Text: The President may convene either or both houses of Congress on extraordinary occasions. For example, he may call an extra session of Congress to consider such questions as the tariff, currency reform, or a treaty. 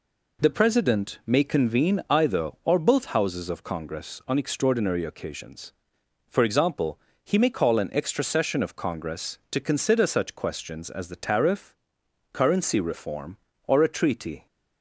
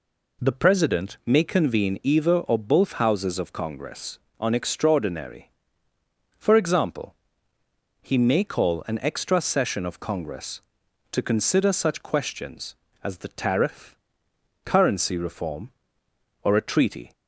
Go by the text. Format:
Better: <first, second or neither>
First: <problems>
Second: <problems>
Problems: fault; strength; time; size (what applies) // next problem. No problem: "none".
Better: first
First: none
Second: skips "occasions"; at 5.9 s